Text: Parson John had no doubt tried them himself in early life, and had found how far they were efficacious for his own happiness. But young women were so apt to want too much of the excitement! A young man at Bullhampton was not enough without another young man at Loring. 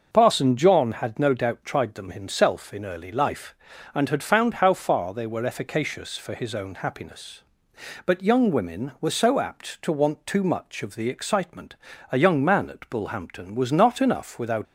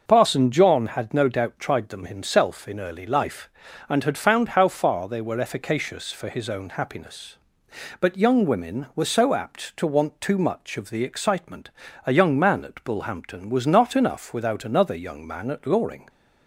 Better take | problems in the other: second | starts louder than the rest; until 1.1 s; 6 dB; noticeable in the second // stops before "another young man at Loring"; at 14.6 s

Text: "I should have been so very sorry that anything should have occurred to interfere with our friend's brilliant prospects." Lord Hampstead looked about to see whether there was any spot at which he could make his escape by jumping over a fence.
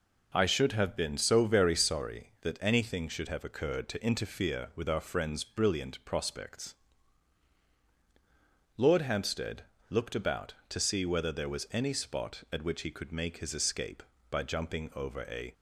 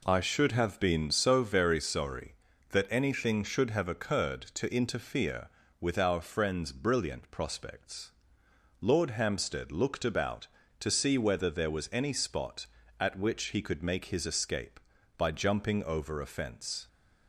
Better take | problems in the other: second | pauses between "Hampstead" and "looked"; slight; at 9.6 s; 0.26 s long // stops before "fence"; at 15.5 s

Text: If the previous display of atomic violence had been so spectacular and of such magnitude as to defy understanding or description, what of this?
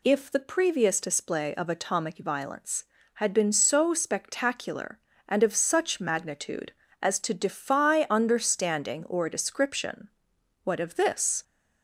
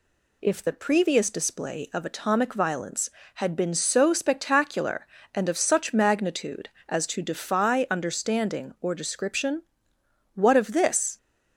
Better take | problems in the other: neither | none

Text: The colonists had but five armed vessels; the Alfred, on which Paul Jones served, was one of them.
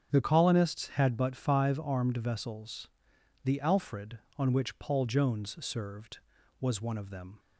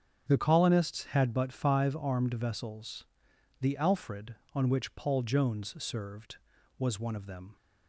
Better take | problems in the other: neither | starts louder than the rest; strong; the same in both

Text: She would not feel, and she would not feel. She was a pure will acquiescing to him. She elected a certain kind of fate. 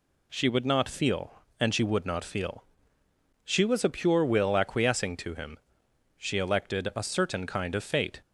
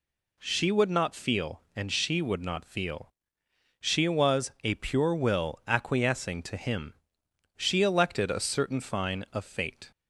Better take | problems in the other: first | says "fine" for "kind"; at 8.8 s

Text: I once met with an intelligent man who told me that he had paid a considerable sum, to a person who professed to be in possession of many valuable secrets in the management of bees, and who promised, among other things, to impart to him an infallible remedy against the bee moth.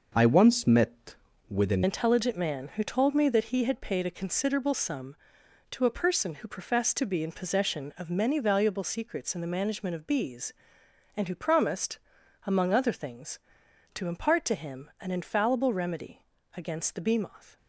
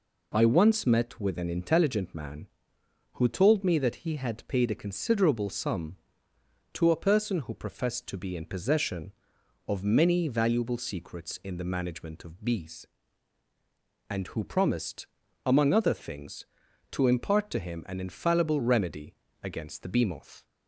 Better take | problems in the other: second | changes voice at "intelligent"; from 1.8 s on; 15.7 s long // pauses between "remedy" and "against"; slight; at 16.2 s; 0.28 s long; slight in the second

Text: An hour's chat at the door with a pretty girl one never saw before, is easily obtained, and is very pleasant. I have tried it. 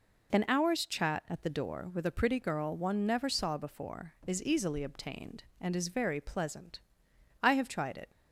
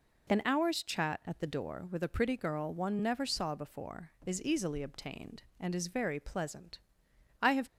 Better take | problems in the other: first | stops before "tried it"; at 7.6 s

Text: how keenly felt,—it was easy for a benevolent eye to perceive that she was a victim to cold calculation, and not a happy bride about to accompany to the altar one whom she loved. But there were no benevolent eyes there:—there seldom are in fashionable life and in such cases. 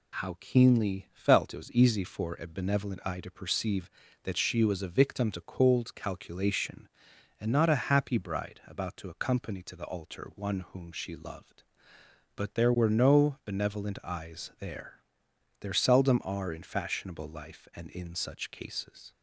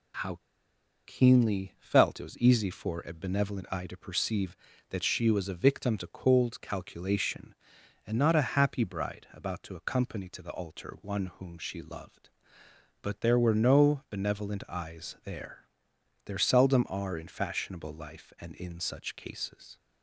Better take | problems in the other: first | pauses between "how" and "keenly"; noticeable; at 0.3 s; 0.69 s long

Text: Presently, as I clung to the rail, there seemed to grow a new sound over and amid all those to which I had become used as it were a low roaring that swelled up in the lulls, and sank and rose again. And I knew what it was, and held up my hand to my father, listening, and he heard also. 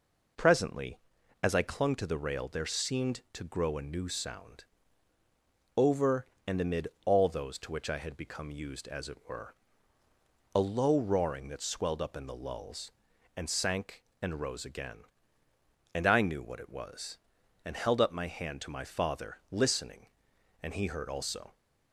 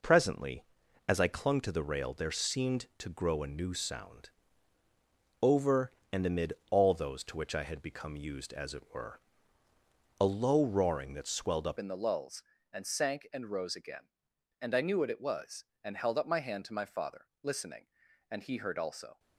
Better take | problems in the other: first | pauses between "sound" and "over"; at 4.3 s; 1.1 s long; also in the first // pauses between "amid" and "all"; slight; at 6.5 s; 0.18 s long; slight in the first // pauses between "were" and "a"; noticeable; at 9.2 s; 0.98 s long; noticeable in the first // changes voice at "in"; from 11.7 s on; 7.4 s long

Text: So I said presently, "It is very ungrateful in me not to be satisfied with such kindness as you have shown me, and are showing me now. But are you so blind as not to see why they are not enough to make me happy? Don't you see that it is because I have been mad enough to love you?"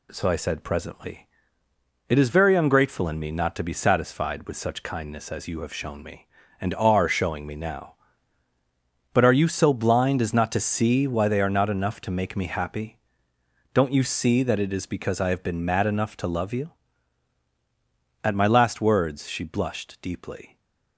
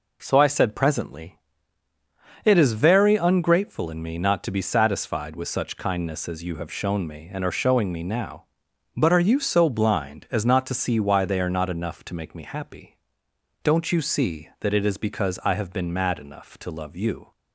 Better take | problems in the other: second | goes on to say "At my last words she blushed deeply"; strong; from 18.2 s on; 2.3 s long

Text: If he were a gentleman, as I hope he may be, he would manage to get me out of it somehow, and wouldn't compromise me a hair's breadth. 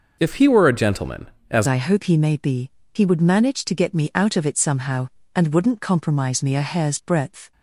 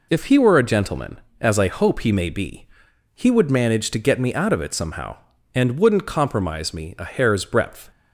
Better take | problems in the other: second | changes voice at "I"; from 1.6 s on; 5.9 s long

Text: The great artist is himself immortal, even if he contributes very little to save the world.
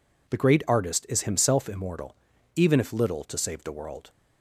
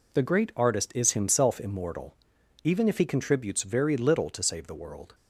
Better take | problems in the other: second | skips "he contributes very"; at 2.9 s

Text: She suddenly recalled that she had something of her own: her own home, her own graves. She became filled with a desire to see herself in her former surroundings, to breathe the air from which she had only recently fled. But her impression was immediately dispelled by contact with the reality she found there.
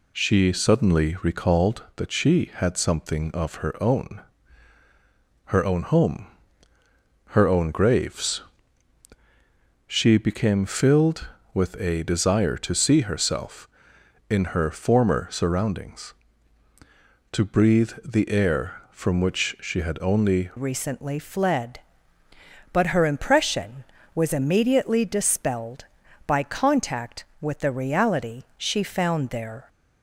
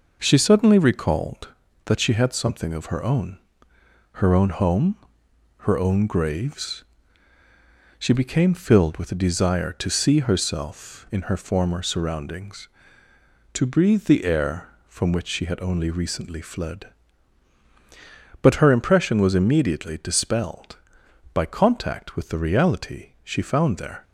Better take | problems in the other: second | changes voice at "recently"; from 20.5 s on; 9.1 s long

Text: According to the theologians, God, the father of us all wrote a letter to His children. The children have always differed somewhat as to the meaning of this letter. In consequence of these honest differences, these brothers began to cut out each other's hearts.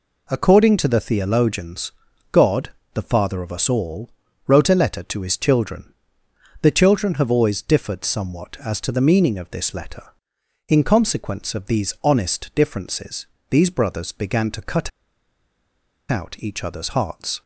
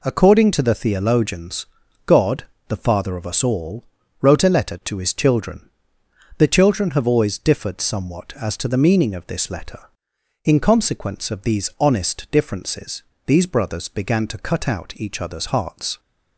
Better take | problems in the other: second | pauses between "all" and "wrote"; slight; at 4.0 s; 0.36 s long; slight in the second // pauses between "cut" and "out"; at 14.8 s; 1.2 s long

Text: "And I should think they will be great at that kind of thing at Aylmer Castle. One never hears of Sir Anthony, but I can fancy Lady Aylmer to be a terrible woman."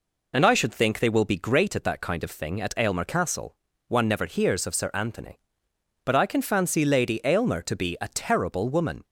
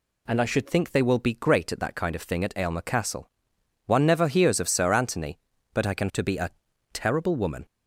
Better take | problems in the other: first | skips "fancy Lady Aylmer"; at 6.1 s // pauses between "a" and "terrible"; at 6.5 s; 0.42 s long

